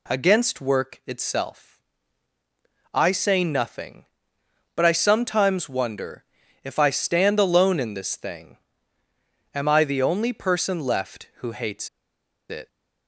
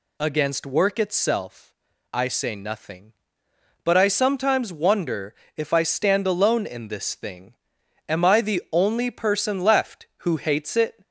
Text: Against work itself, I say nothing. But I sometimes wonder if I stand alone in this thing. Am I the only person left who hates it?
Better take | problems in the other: second | pauses between "wonder" and "if"; at 6.2 s; 0.40 s long; slight in the second // pauses between "hates" and "it"; noticeable; at 11.8 s; 0.60 s long

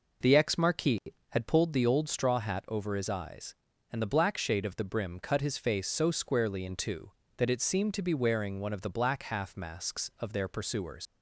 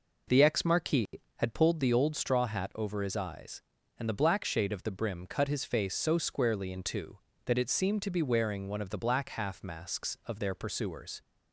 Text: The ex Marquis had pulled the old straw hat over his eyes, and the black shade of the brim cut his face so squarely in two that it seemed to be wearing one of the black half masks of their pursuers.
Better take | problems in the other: second | leaves "pursuers" unfinished; at 11.0 s; 90 ms

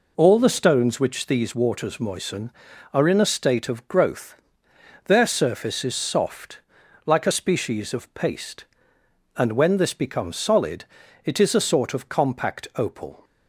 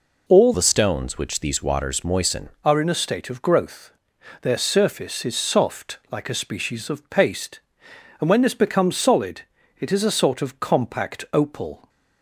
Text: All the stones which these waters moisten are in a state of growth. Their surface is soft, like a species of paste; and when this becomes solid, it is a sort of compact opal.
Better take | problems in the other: first | changes voice from "the" to "moisten"; from 0.5 to 2.4 s; 1.9 s long

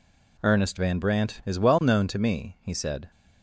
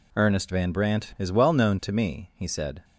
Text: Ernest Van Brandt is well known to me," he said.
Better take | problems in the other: neither | none

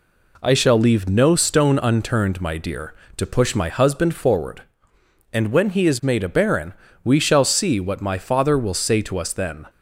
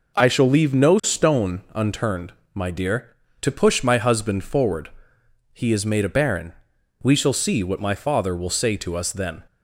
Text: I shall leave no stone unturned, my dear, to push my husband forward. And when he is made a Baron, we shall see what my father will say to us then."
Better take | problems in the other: first | skips "And when"; at 5.2 s

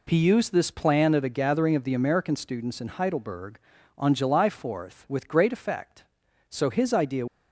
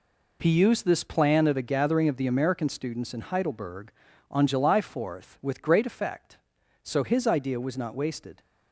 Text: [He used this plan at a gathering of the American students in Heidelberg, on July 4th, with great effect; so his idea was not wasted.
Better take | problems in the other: second | stops before "was not wasted"; at 7.2 s

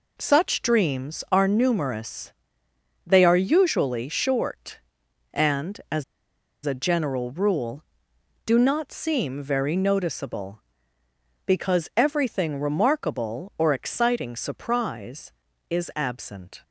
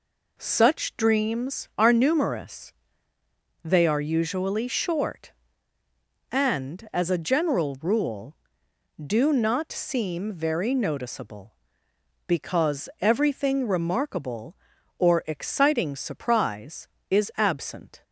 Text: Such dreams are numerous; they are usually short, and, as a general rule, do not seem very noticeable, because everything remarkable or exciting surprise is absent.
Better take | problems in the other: second | pauses between "as" and "a"; noticeable; at 6.0 s; 0.62 s long

